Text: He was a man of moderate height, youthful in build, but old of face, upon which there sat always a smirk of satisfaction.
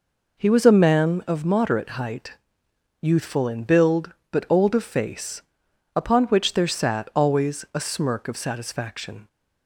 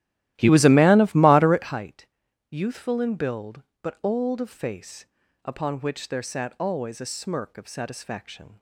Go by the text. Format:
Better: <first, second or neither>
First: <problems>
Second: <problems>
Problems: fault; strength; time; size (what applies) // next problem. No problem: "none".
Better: first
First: none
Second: starts louder than the rest; strong; until 1.8 s; 14.5 dB